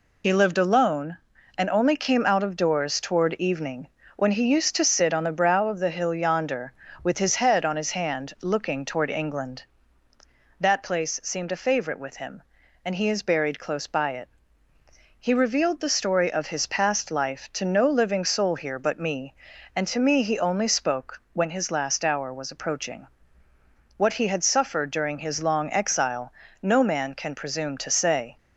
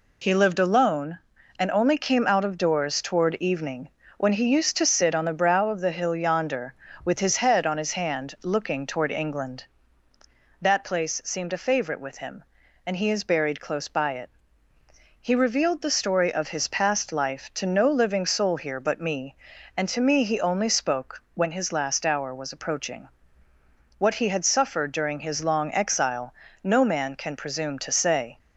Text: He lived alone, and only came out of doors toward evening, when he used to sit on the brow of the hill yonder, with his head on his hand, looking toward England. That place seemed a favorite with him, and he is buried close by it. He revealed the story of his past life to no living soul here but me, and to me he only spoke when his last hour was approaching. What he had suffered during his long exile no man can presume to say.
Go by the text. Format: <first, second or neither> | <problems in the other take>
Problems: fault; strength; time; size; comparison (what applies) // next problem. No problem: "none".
second | loses the start of "He"; at 0.2 s; 45 ms // pauses between "exile" and "no"; slight; at 26.3 s; 0.30 s long; slight in the second